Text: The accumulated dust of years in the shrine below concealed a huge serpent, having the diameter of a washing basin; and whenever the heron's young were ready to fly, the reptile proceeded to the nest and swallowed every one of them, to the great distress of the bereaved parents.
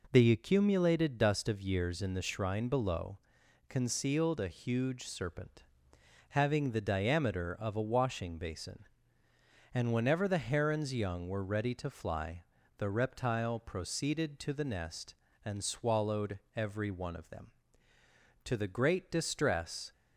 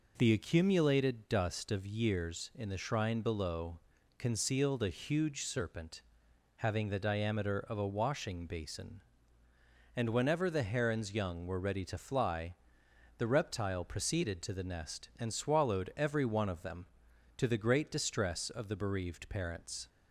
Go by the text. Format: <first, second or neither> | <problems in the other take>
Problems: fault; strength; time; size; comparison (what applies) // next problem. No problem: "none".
second | pauses between "below" and "concealed"; noticeable; at 3.1 s; 0.50 s long; slight in the second // pauses between "swallowed" and "every"; slight; at 16.3 s; 0.18 s long // stops before "of the bereaved parents"; at 19.9 s